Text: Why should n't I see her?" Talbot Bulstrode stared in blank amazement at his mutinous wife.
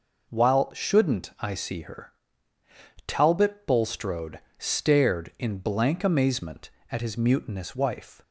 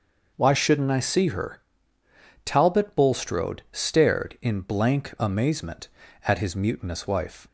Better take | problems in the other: second | says "While" for "Why"; at 0.2 s // pauses between "Bulstrode" and "stared"; slight; at 4.3 s; 0.18 s long

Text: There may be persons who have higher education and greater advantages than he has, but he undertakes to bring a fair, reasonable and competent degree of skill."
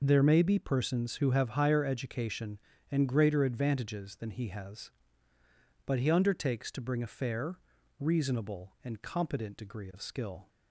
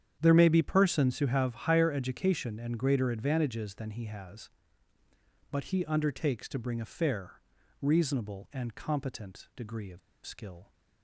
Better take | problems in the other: first | starts louder than the rest; strong; until 1.2 s; 9 dB // pauses between "of" and "skill"; slight; at 9.9 s; 0.26 s long

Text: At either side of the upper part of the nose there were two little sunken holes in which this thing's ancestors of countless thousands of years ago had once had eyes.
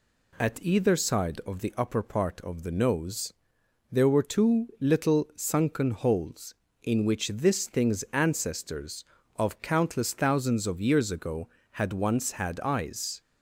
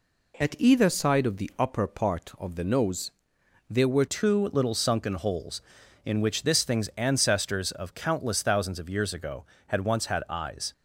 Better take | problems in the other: first | pauses between "nose" and "there"; noticeable; at 3.1 s; 0.58 s long; noticeable in the first // changes voice at "two"; from 4.0 s on; 6.7 s long

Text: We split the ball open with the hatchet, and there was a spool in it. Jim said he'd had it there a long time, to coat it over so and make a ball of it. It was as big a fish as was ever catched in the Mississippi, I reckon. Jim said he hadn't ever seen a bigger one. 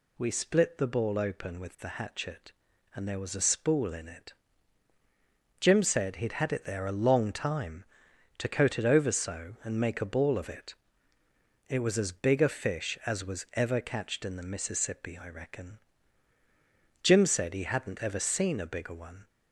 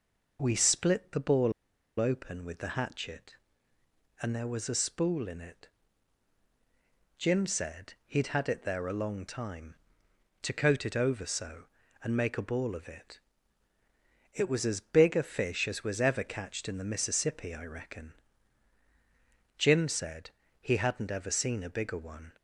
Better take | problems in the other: first | pauses between "ball" and "open"; noticeable; at 1.5 s; 0.47 s long // pauses between "said" and "he"; slight; at 20.2 s; 0.30 s long

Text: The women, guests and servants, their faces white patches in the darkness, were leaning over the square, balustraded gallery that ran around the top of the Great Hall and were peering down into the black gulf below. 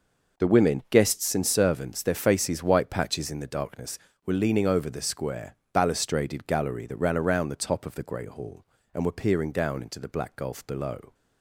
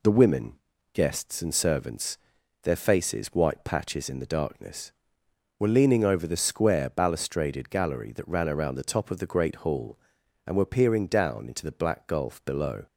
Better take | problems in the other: neither | none

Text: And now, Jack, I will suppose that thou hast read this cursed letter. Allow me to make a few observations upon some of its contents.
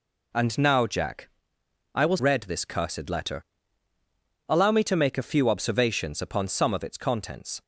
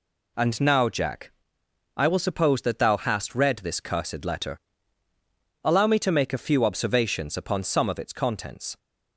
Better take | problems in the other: second | skips "suppose that thou hast"; at 2.1 s

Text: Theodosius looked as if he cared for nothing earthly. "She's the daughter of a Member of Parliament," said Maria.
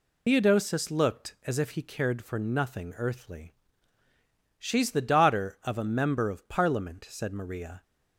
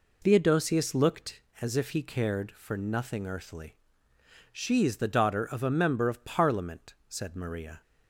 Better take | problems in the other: second | loses the start of "Theodosius"; at 0.2 s; 85 ms

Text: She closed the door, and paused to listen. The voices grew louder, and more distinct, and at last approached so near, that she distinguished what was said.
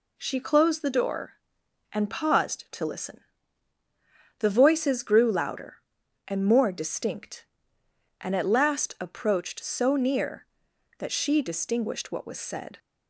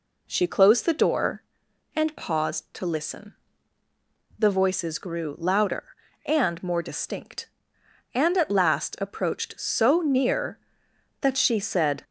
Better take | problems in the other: first | skips "distinguished what was"; at 11.5 s

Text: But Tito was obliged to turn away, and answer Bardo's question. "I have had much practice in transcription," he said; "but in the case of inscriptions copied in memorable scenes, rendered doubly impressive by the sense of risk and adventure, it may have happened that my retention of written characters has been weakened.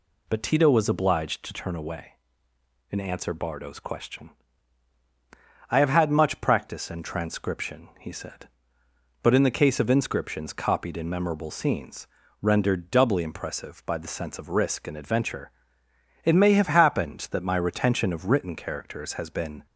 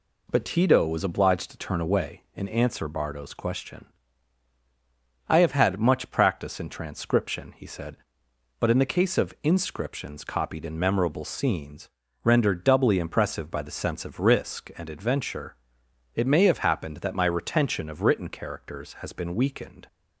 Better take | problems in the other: second | stops before "weakened"; at 19.6 s

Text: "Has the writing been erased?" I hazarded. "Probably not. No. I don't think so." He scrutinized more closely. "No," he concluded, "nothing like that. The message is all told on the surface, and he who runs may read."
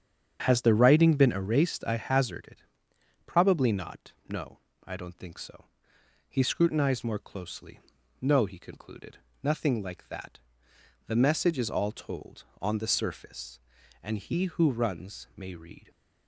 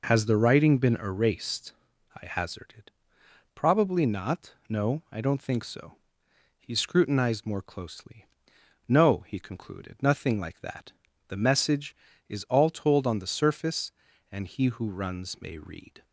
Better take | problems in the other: second | starts louder than the rest; strong; until 1.6 s; 8 dB

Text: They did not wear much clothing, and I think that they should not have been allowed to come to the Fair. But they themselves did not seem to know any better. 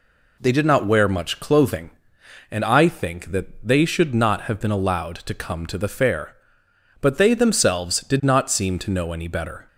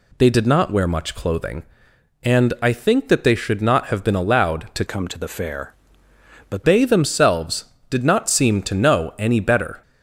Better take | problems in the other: first | changes voice from "come" to "But"; from 4.8 to 6.6 s; 1.8 s long

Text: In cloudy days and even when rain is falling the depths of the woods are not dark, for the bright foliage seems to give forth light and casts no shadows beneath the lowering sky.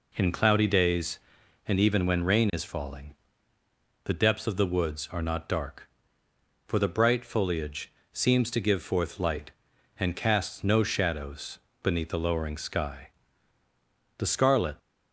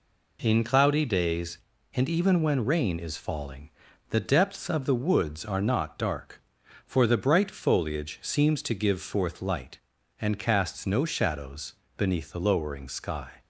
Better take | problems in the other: second | pauses between "falling" and "the"; noticeable; at 3.1 s; 0.90 s long; also in the second // pauses between "foliage" and "seems"; slight; at 7.9 s; 0.22 s long // pauses between "shadows" and "beneath"; slight; at 11.5 s; 0.24 s long; slight in the second // goes on to say "The scarlet"; from 14.1 s on; 0.58 s long

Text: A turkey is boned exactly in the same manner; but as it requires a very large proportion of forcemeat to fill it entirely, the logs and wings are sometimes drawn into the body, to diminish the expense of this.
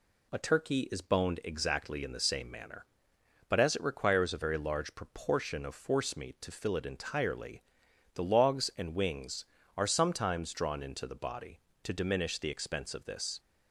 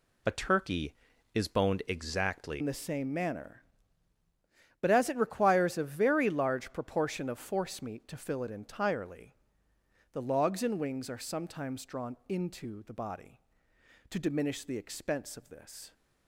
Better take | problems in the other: first | changes voice at "in"; from 2.6 s on; 13.3 s long

